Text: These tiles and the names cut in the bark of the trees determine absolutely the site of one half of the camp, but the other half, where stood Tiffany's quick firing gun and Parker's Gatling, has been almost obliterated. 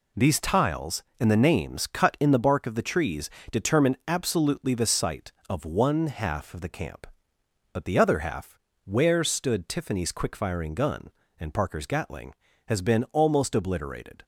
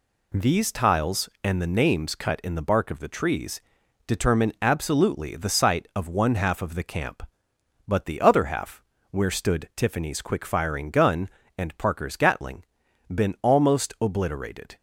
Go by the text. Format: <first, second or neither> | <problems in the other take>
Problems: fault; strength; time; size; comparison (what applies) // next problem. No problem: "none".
first | pauses between "trees" and "determine"; noticeable; at 3.6 s; 0.46 s long; slight in the first // skips "has"; at 12.8 s